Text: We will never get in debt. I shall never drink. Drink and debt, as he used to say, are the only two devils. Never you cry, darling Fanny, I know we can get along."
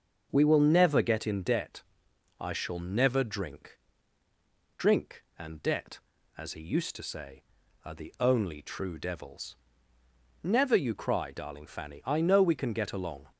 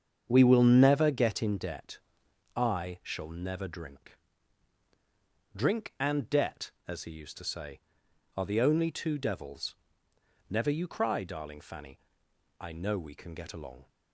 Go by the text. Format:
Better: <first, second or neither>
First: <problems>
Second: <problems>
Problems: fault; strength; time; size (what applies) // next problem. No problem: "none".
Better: second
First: starts louder than the rest; until 1.3 s; 6 dB // says "true" for "two"; at 8.6 s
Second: starts louder than the rest; strong; until 1.2 s; 7.5 dB